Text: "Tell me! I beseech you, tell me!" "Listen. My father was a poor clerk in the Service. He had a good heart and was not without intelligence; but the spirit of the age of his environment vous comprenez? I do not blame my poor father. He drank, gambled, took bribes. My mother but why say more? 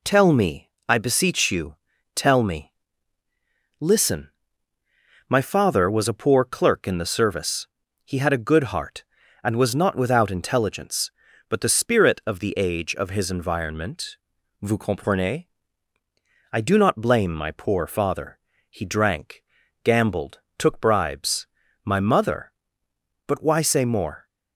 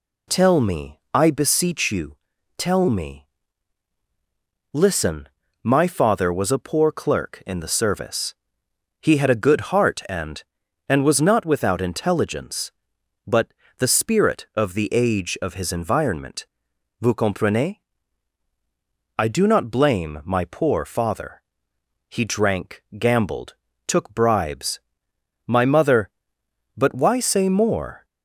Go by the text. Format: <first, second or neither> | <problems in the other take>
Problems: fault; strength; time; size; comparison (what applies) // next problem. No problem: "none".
first | says "and" twice; at 10.8 s // pauses between "but" and "the"; slight; at 13.4 s; 0.32 s long // pauses between "environment" and "vous"; noticeable; at 16.4 s; 0.56 s long; noticeable in the first